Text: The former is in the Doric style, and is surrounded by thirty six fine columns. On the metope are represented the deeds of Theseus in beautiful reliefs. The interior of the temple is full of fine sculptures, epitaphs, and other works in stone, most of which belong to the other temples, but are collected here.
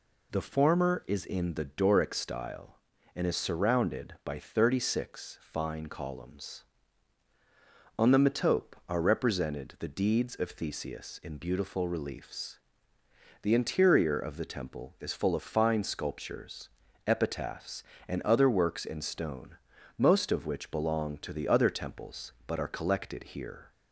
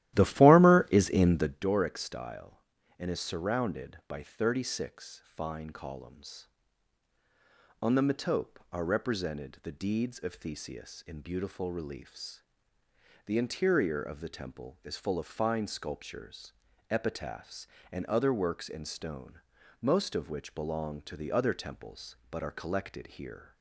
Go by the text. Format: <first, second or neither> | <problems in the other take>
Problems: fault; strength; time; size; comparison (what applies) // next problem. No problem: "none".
first | starts louder than the rest; strong; until 1.7 s; 14 dB